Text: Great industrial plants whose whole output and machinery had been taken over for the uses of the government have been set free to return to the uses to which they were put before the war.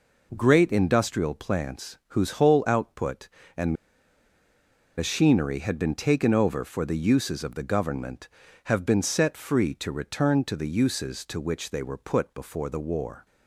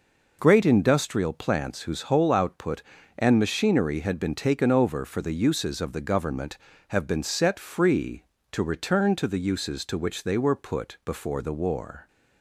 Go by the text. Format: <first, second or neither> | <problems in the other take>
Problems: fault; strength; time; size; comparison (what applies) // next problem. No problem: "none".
second | pauses between "and" and "machinery"; at 3.7 s; 1.2 s long